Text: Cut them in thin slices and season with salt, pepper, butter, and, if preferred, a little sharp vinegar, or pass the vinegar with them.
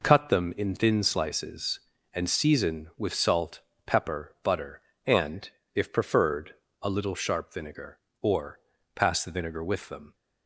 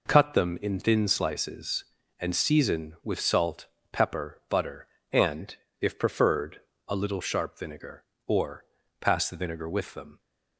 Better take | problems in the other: neither | pauses between "or" and "pass"; slight; the same in both

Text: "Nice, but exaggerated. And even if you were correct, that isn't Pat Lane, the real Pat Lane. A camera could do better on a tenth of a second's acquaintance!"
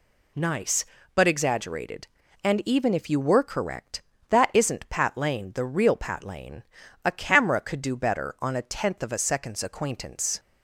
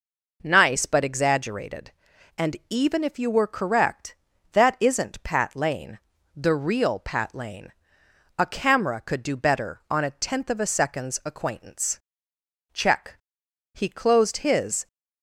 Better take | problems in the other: first | goes on to say "Check He closed his"; strong; from 12.7 s on; 2.1 s long

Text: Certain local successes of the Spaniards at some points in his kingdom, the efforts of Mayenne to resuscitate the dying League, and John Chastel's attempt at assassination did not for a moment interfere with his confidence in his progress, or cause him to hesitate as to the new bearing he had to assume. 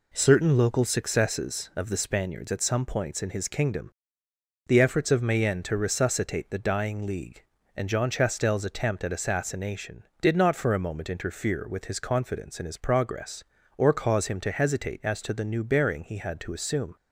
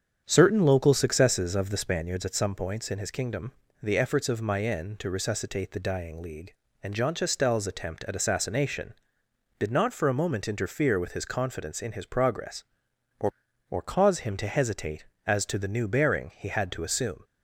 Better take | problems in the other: first | starts louder than the rest; strong; until 1.2 s; 8 dB // says "or" twice; at 13.6 s

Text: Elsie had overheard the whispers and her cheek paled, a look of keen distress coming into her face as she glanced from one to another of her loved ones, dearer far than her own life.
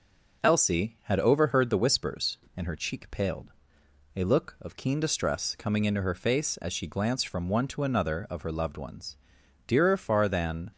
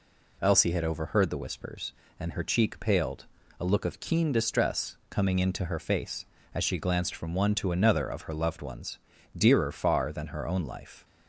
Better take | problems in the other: second | stops before "her own life"; at 10.7 s

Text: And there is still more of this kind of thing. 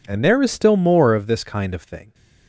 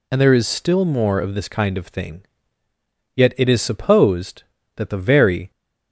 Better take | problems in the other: first | goes on to say "Yet it is supposed that the very"; strong; from 3.1 s on; 2.3 s long

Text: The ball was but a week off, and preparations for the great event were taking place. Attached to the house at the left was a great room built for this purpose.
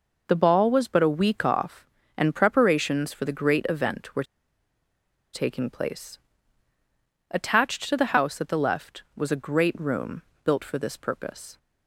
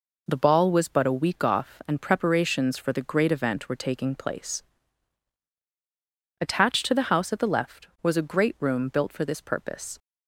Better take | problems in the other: second | pauses between "were" and "taking"; at 4.2 s; 1.0 s long // pauses between "room" and "built"; slight; at 10.2 s; 0.22 s long

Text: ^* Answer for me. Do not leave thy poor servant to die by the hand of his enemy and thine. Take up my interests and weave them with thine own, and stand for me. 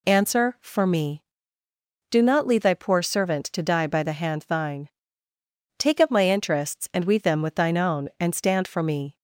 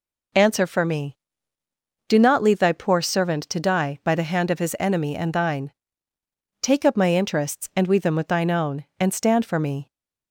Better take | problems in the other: second | skips "of his enemy and"; at 4.4 s

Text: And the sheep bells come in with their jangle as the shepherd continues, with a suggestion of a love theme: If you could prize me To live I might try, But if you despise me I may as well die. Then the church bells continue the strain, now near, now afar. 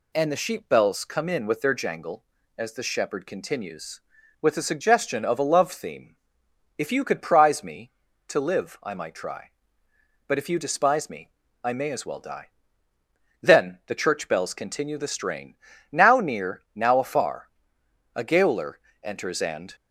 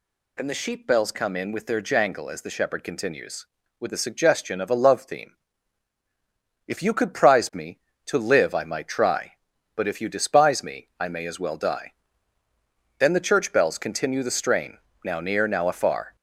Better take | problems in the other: second | pauses between "me" and "I"; slight; at 11.3 s; 0.34 s long // goes on to say "A gaoler enters and"; from 18.1 s on; 1.6 s long

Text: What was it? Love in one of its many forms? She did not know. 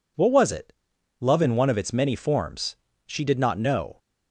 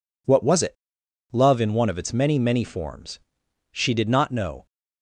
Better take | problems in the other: first | says "many" twice; at 2.3 s

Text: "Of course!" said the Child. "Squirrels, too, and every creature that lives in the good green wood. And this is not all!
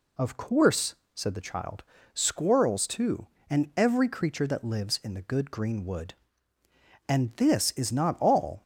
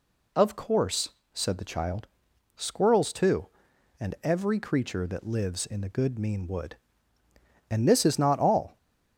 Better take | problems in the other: first | says "mean" for "green"; at 6.2 s

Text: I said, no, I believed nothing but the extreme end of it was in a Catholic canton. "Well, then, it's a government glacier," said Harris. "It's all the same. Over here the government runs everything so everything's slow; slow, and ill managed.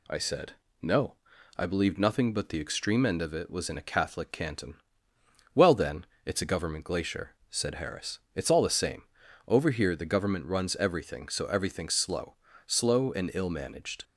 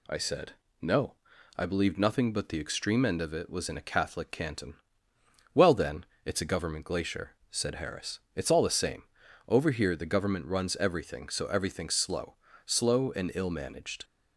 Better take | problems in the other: neither | none

